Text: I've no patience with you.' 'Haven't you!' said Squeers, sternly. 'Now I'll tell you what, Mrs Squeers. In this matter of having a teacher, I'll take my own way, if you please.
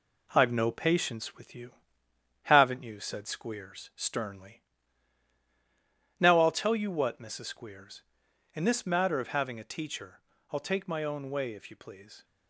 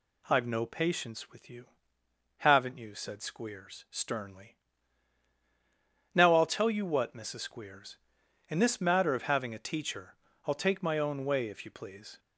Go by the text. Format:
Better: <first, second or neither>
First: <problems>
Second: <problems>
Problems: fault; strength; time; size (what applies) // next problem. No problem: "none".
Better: second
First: gets quieter; noticeable; throughout; 4.5 dB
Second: none